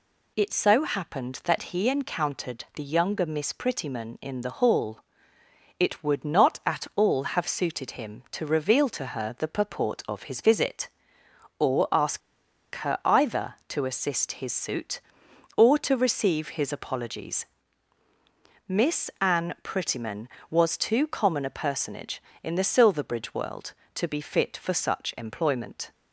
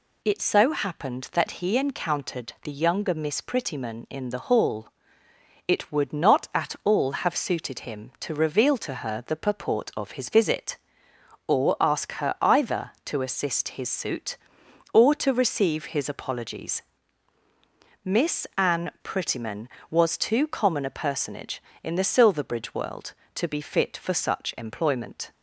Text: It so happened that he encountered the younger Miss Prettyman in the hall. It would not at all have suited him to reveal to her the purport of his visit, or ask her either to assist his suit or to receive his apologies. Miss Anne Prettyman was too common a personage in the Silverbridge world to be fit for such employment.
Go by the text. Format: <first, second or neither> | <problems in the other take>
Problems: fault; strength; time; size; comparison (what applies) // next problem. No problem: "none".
second | pauses between "ask" and "her"; noticeable; at 12.2 s; 0.56 s long